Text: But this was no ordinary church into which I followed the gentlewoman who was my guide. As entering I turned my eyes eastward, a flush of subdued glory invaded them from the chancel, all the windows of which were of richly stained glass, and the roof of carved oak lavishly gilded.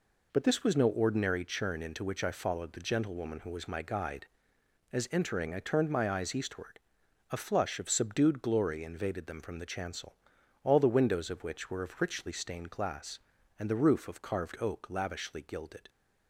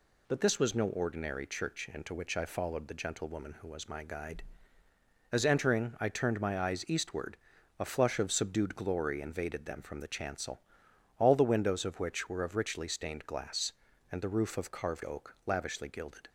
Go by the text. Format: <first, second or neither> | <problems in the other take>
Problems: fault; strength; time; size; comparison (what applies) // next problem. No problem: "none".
second | says "churn" for "church"; at 1.4 s